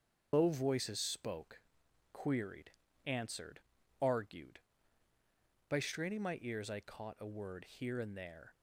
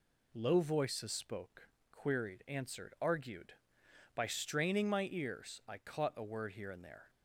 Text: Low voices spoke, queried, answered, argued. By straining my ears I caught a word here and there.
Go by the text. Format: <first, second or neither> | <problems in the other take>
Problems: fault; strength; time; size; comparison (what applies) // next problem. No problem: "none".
second | loses the start of "Low"; at 0.3 s; 130 ms // starts louder than the rest; until 1.3 s; 6.5 dB